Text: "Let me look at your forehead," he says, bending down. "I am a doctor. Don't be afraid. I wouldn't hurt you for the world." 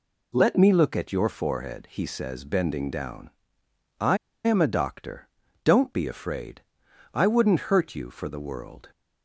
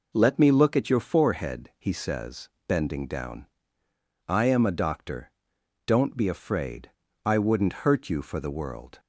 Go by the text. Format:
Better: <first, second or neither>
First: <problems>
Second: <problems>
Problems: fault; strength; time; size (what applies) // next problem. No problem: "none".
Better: second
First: pauses between "I" and "am"; slight; at 4.1 s; 0.27 s long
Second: none